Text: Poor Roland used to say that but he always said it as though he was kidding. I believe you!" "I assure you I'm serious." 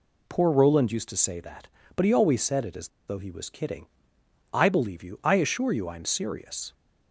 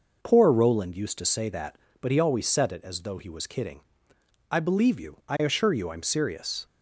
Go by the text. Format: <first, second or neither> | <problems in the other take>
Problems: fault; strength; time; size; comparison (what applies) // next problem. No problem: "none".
second | pauses between "as" and "though"; slight; at 2.8 s; 0.19 s long